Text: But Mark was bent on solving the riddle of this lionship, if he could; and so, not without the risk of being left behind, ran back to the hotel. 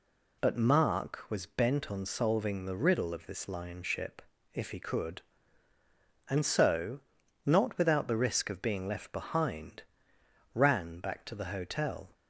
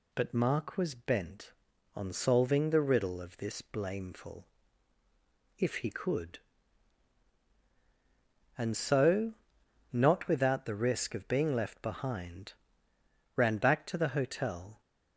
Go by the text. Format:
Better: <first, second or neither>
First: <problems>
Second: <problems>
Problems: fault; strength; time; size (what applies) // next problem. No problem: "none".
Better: first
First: none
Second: says "blameful" for "lionship"; at 3.6 s